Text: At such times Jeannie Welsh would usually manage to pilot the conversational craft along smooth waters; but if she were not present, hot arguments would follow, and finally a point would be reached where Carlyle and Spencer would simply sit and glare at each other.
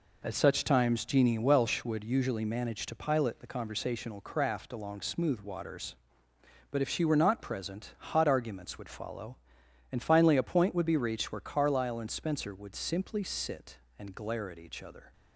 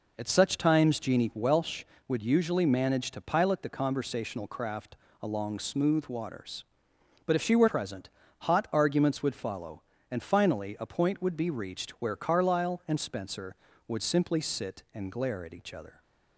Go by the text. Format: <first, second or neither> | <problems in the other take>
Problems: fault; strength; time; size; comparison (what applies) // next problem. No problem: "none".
first | pauses between "craft" and "along"; slight; at 4.9 s; 0.26 s long // skips "not"; at 7.6 s